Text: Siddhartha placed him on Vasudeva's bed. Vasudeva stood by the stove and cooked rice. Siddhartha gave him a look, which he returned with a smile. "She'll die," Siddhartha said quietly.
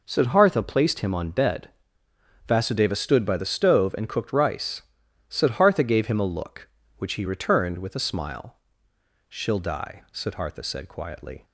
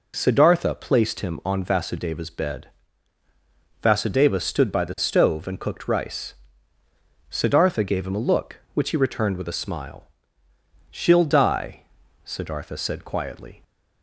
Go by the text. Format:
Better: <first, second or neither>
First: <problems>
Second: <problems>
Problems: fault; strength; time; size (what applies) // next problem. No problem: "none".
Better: second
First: skips "Vasudeva's"; at 1.2 s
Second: none